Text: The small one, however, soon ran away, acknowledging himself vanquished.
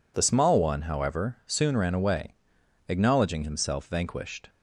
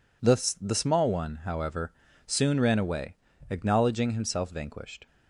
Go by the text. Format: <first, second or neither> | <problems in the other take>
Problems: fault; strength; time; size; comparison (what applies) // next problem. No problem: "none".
first | says "The" twice; at 0.6 s